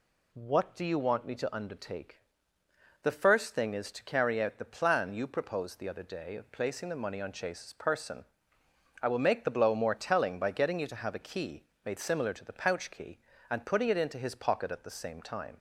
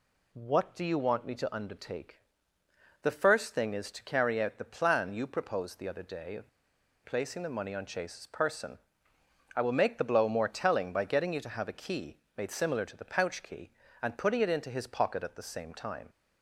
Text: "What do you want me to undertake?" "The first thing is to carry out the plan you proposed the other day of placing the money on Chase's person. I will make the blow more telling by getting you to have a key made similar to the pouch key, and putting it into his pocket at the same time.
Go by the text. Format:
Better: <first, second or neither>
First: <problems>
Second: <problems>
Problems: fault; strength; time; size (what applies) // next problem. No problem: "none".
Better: first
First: pauses between "key" and "made"; slight; at 11.6 s; 0.21 s long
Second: pauses between "of" and "placing"; noticeable; at 6.4 s; 0.56 s long // pauses between "key" and "made"; slight; at 12.1 s; 0.20 s long